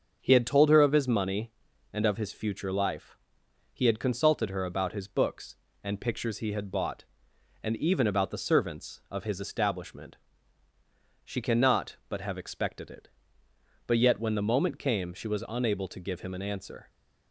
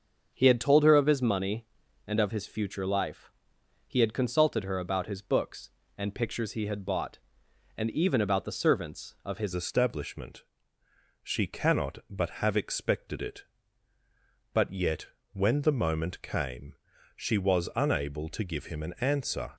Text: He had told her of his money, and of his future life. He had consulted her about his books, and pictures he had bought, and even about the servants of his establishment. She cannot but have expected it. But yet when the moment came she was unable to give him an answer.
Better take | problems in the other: first | starts louder than the rest; until 1.3 s; 6.5 dB; also in the first // changes voice at "establishment"; from 9.5 s on; 10.0 s long // pauses between "yet" and "when"; slight; at 15.0 s; 0.26 s long // pauses between "came" and "she"; at 16.7 s; 0.40 s long

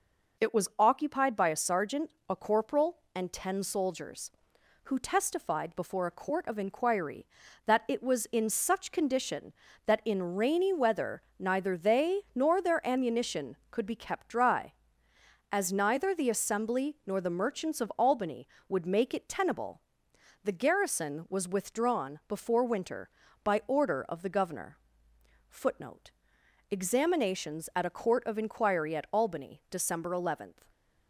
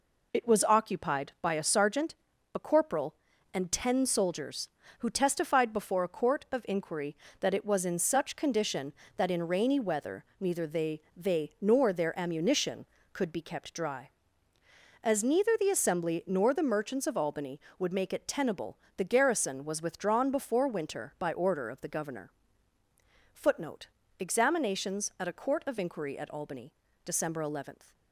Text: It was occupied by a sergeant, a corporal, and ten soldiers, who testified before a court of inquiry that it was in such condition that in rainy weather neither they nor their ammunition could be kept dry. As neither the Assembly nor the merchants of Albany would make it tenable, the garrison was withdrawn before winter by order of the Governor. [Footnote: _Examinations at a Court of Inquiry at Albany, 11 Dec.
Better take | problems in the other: first | pauses between "weather" and "neither"; slight; at 10.2 s; 0.16 s long; slight in the first // says "they" twice; at 11.1 s

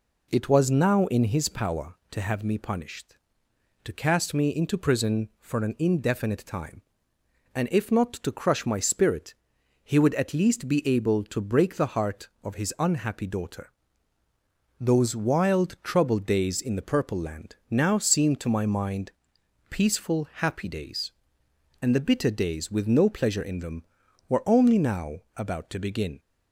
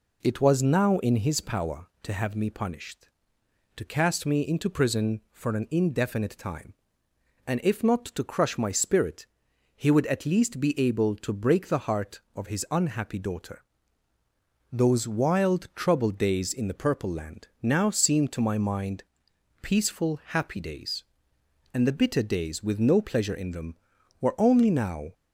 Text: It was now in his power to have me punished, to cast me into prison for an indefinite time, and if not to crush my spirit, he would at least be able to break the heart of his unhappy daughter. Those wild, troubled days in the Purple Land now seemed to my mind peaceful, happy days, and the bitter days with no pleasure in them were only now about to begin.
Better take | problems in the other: first | pauses between "Land" and "now"; slight; at 17.4 s; 0.16 s long; slight in the first // pauses between "mind" and "peaceful"; noticeable; at 19.0 s; 0.62 s long; noticeable in the first // stops before "about to begin"; at 25.1 s

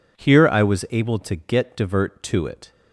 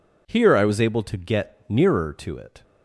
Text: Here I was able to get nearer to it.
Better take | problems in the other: second | says "divert" for "nearer"; at 1.7 s

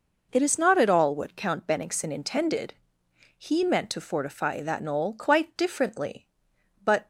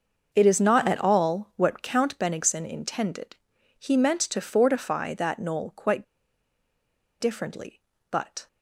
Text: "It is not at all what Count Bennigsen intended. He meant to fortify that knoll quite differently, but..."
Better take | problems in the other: first | starts louder than the rest; until 1.3 s; 6 dB // pauses between "quite" and "differently"; at 6.0 s; 1.1 s long

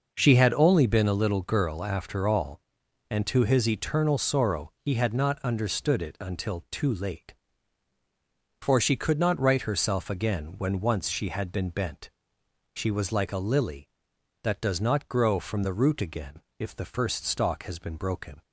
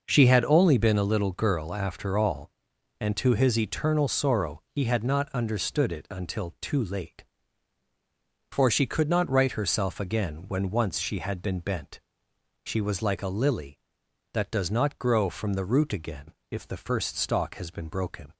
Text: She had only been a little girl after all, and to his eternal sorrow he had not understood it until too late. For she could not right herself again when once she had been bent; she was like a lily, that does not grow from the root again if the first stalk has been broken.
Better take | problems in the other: neither | pauses between "again" and "if"; slight; the same in both

